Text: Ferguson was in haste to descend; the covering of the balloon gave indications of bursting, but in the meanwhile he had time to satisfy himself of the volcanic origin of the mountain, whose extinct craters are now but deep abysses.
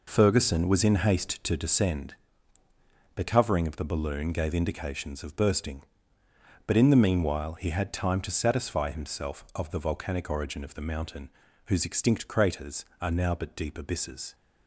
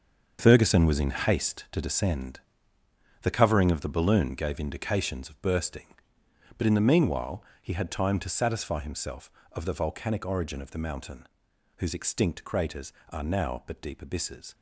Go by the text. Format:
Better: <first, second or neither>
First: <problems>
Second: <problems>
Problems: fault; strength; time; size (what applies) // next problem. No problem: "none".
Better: first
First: none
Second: gets quieter; strong; throughout; 10.5 dB // pauses between "meanwhile" and "he"; slight; at 7.4 s; 0.16 s long